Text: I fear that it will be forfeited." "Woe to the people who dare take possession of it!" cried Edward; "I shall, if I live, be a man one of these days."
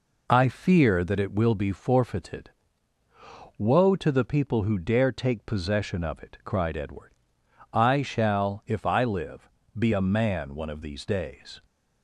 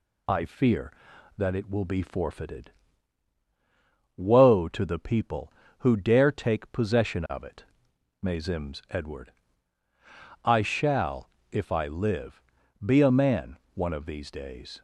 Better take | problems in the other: first | says "mazims" for "cried"; at 8.2 s // pauses between "man" and "one"; slight; at 13.5 s; 0.20 s long

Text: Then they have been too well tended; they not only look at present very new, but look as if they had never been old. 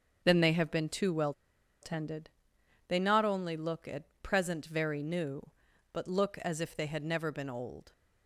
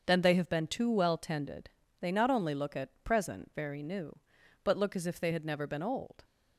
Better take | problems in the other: second | starts louder than the rest; until 1.2 s; 6.5 dB; also in the second // pauses between "well" and "tended"; noticeable; at 1.3 s; 0.49 s long // pauses between "at" and "present"; slight; at 4.0 s; 0.18 s long

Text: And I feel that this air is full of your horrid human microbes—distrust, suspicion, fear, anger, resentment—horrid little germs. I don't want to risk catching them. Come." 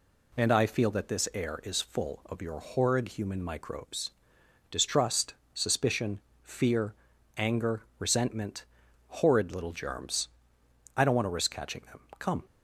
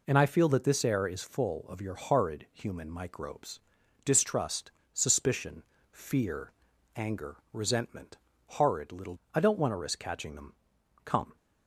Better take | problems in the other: first | skips "germs"; at 9.2 s

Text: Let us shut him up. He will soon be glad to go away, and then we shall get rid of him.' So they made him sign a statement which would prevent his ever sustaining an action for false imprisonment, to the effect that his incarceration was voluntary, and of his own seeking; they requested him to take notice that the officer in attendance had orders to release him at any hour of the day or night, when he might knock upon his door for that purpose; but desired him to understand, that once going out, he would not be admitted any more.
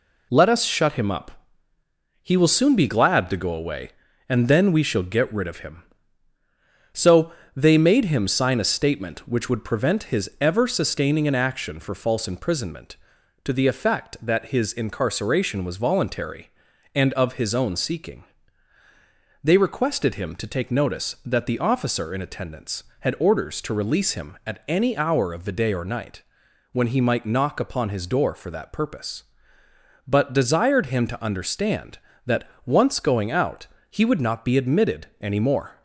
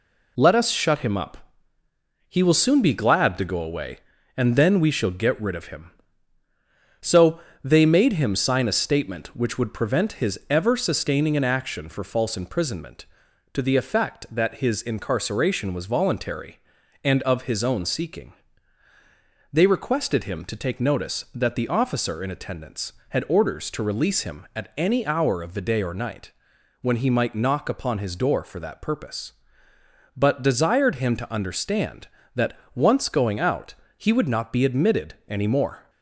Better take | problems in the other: neither | pauses between "So" and "they"; slight; the same in both // pauses between "that" and "once"; slight; the same in both

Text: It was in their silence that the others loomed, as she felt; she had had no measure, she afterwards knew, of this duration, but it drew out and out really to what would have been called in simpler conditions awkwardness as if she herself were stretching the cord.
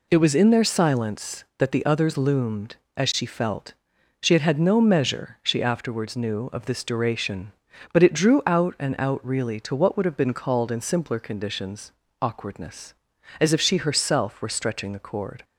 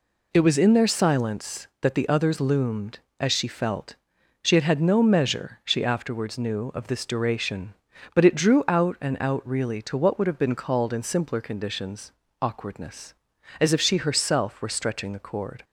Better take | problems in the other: neither | pauses between "conditions" and "awkwardness"; slight; the same in both

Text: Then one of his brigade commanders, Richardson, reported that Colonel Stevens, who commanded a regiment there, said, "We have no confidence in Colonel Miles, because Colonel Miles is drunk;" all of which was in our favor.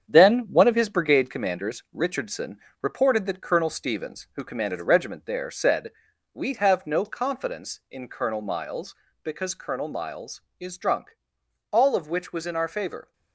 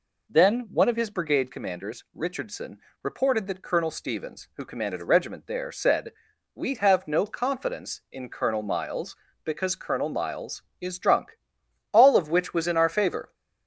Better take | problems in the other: second | gets quieter; throughout; 6.5 dB

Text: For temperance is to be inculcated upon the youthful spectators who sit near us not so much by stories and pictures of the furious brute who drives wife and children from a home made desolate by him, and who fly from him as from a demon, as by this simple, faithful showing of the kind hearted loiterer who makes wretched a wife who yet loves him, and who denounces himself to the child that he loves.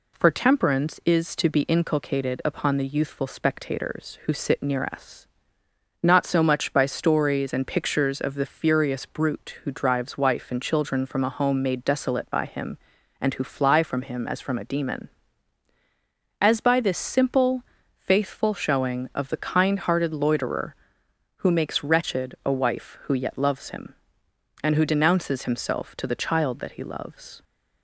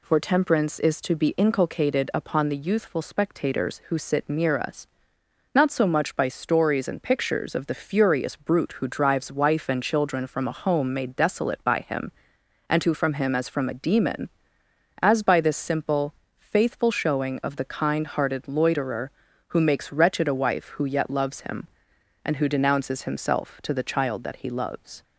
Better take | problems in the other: first | pauses between "us" and "not"; noticeable; at 4.8 s; 0.70 s long; noticeable in the first // skips "fly"; at 12.9 s

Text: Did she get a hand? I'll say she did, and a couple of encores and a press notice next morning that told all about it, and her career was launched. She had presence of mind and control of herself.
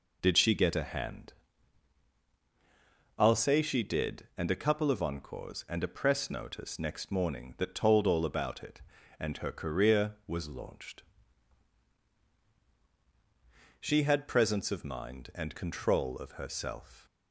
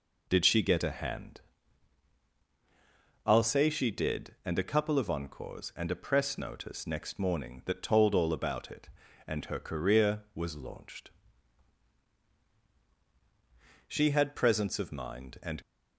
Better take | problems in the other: first | stops before "control of herself"; at 15.6 s

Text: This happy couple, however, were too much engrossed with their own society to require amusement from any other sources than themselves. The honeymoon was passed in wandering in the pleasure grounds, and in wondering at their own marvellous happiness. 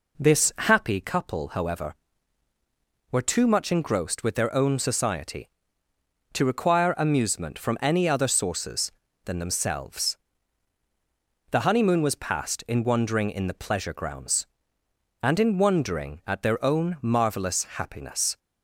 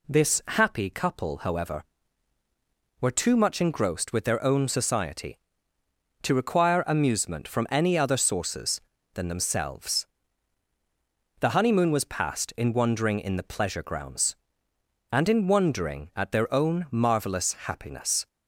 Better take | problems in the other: second | starts louder than the rest; until 1.1 s; 4 dB

